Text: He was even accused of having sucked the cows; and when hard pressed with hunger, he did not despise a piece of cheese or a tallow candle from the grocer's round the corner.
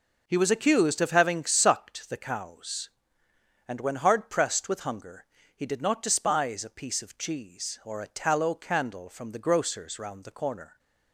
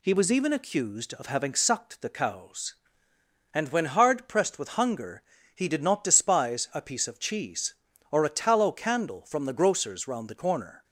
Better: second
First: skips "even"; at 0.5 s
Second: none

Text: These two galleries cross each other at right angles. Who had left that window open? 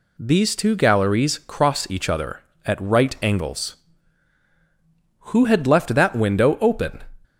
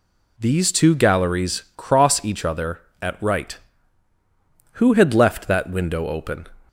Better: first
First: none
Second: skips "angles"; at 4.1 s

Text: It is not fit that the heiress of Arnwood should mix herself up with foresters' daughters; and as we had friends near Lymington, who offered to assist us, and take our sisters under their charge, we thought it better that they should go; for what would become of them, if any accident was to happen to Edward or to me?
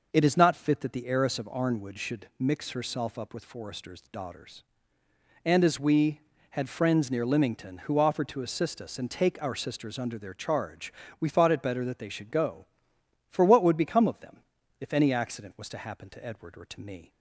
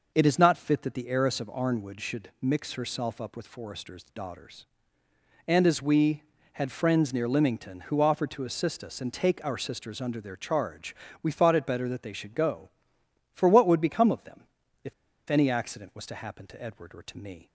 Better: first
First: none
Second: pauses between "if" and "any"; at 14.9 s; 0.36 s long

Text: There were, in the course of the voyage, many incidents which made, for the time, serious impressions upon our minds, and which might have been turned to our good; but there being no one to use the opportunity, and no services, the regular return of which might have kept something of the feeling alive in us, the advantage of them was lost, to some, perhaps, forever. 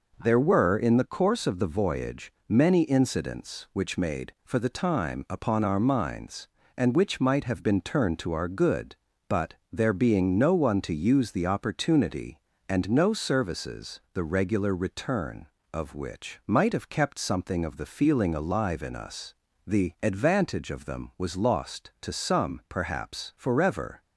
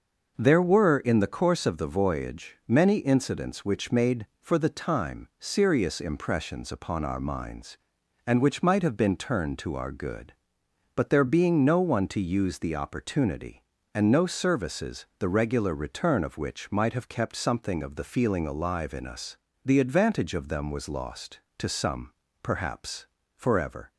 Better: second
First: skips "serious impressions"; at 5.2 s // pauses between "but" and "there"; slight; at 9.5 s; 0.18 s long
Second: none

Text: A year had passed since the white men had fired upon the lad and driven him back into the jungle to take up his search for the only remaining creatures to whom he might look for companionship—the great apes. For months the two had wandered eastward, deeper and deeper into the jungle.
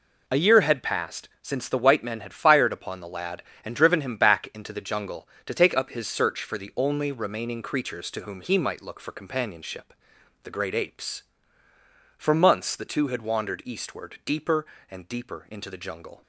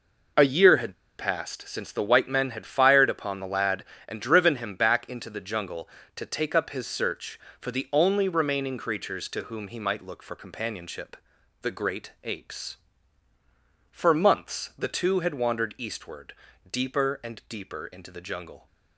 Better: first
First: none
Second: pauses between "had" and "passed"; slight; at 0.9 s; 0.22 s long

